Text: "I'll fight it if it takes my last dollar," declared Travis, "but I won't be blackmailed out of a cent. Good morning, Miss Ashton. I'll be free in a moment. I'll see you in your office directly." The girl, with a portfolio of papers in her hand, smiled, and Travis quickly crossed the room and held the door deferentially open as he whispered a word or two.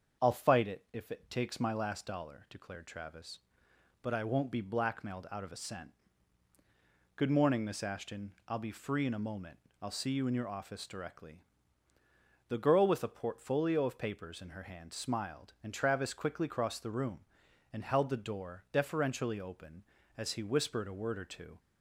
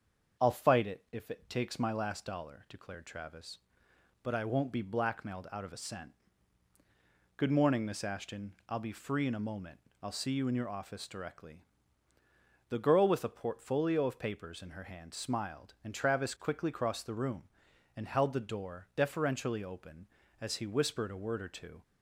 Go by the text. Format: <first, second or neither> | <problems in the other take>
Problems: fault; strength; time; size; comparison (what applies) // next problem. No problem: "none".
neither | starts louder than the rest; the same in both